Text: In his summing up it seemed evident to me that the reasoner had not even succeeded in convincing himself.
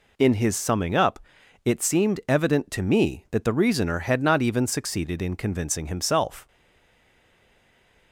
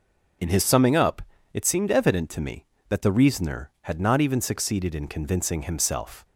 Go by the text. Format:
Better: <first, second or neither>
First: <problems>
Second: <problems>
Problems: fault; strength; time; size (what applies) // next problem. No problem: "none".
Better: second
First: pauses between "up" and "it"; noticeable; at 1.1 s; 0.46 s long // stays silent after the last word; noticeable; from 6.4 s on; 1.7 s long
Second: pauses between "up" and "it"; slight; at 1.2 s; 0.32 s long